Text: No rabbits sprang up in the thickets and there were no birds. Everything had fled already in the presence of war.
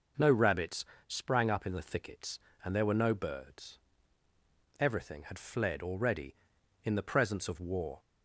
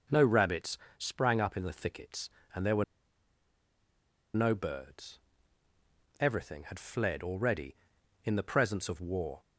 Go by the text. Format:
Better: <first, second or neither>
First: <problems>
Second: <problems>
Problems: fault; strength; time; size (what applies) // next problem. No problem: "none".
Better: first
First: pauses between "rabbits" and "sprang"; slight; at 0.8 s; 0.22 s long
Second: pauses between "rabbits" and "sprang"; slight; at 0.7 s; 0.20 s long // pauses between "were" and "no"; strong; at 2.8 s; 1.5 s long